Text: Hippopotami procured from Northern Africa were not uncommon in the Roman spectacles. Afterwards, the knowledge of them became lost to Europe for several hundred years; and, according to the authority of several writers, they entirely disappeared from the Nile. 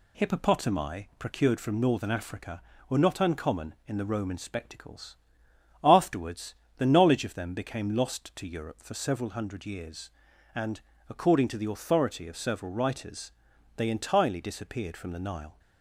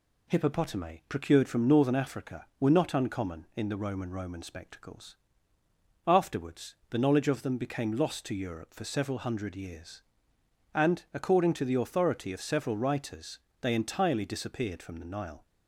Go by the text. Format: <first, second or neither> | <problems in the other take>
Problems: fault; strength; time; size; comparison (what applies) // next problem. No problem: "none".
first | says "Roman" twice; at 4.0 s